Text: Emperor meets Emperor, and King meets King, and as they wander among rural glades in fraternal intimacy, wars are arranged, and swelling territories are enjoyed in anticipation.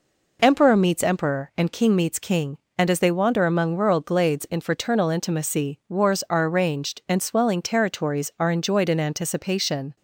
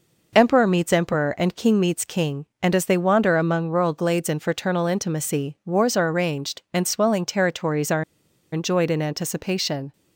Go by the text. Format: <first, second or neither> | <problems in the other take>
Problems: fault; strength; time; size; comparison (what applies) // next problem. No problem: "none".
first | pauses between "are" and "enjoyed"; noticeable; at 8.0 s; 0.48 s long